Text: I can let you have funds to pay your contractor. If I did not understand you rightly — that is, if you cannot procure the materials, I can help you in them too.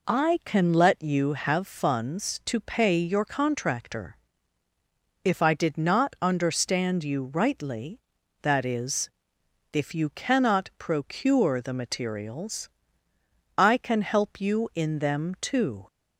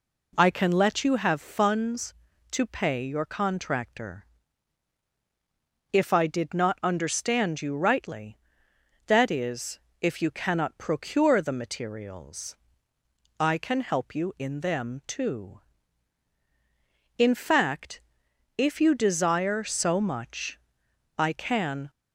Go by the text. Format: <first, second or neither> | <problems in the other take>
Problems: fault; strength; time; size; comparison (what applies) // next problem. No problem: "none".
first | goes on to say "In fact if you desire so much I can"; strong; from 17.1 s on; 4.7 s long